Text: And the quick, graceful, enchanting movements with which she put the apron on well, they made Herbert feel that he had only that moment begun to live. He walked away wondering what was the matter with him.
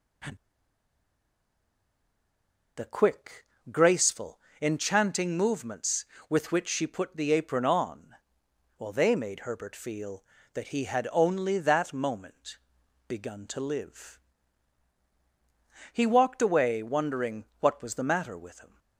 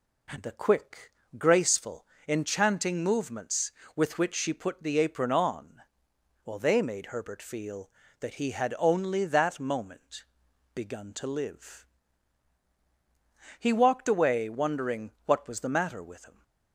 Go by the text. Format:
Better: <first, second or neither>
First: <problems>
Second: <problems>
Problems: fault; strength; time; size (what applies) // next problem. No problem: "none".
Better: second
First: pauses between "And" and "the"; strong; at 0.3 s; 2.4 s long // pauses between "on" and "well"; noticeable; at 8.1 s; 0.64 s long // pauses between "moment" and "begun"; noticeable; at 12.5 s; 0.48 s long // pauses between "wondering" and "what"; slight; at 17.4 s; 0.16 s long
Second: pauses between "on" and "well"; noticeable; at 5.8 s; 0.64 s long // pauses between "moment" and "begun"; noticeable; at 10.2 s; 0.48 s long // pauses between "wondering" and "what"; slight; at 15.1 s; 0.15 s long